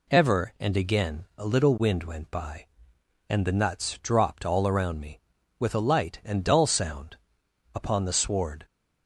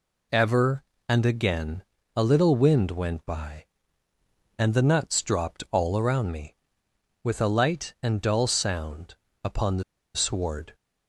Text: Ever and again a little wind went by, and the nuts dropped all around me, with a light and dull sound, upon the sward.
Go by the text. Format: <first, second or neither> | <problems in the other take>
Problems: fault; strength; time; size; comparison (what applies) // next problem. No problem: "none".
first | pauses between "again" and "a"; slight; at 1.8 s; 0.32 s long // pauses between "the" and "sward"; slight; at 9.8 s; 0.33 s long